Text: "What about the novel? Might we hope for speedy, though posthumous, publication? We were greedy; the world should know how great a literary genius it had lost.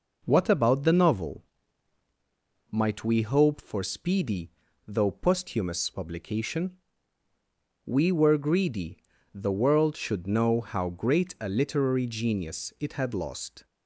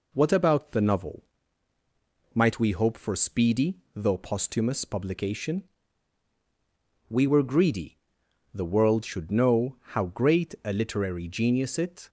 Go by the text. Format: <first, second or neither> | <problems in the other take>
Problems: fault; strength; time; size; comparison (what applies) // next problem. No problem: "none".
first | pauses between "know" and "how"; slight; at 9.7 s; 0.16 s long // stops before "had lost"; at 12.0 s